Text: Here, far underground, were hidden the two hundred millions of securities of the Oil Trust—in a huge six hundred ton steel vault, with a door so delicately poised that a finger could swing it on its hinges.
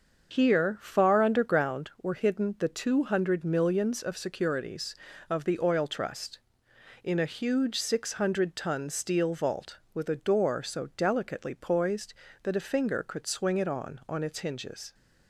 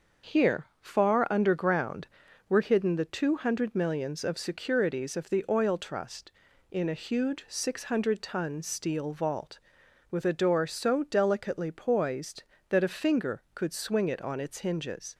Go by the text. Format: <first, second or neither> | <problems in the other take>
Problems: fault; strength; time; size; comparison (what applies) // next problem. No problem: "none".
second | starts louder than the rest; until 1.3 s; 6.5 dB; also in the second // says "on" twice; at 14.0 s